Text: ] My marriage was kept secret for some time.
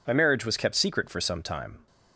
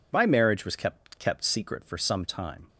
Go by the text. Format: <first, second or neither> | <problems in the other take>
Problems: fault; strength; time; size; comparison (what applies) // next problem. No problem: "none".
first | says "kept" twice; at 1.1 s